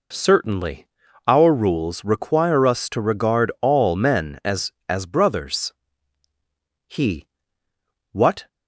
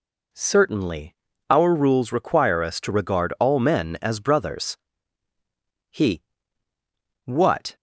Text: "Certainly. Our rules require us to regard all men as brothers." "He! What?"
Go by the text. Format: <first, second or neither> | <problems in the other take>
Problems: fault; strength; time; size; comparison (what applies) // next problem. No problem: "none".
second | says "as" twice; at 4.8 s